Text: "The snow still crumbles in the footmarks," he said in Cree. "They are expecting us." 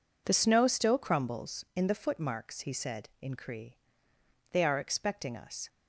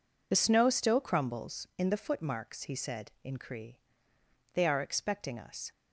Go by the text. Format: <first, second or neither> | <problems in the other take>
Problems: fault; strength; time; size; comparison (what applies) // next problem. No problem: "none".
first | loses the start of "The"; at 0.3 s; 25 ms